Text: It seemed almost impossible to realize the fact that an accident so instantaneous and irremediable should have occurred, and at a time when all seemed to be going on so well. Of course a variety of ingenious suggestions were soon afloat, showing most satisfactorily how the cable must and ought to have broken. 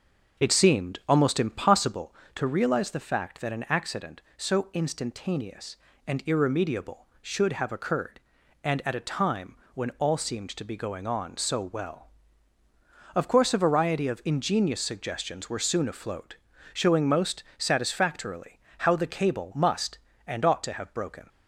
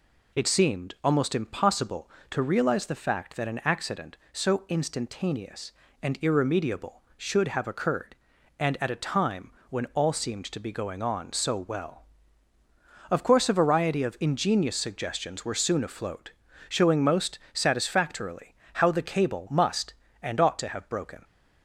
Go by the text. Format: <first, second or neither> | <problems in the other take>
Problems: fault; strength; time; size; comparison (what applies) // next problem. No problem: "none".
second | starts louder than the rest; noticeable; until 2.0 s; 6 dB // pauses between "time" and "when"; slight; at 9.5 s; 0.18 s long; slight in the second // pauses between "most" and "satisfactorily"; slight; at 17.4 s; 0.16 s long; slight in the second // pauses between "satisfactorily" and "how"; slight; at 18.5 s; 0.20 s long; slight in the second